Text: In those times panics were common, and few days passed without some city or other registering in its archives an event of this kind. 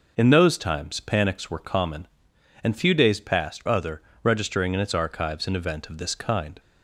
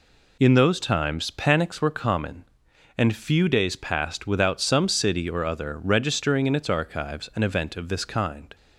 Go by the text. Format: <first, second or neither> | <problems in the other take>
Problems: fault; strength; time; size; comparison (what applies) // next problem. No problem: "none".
second | skips "without some city or"; at 3.6 s // pauses between "other" and "registering"; slight; at 4.0 s; 0.22 s long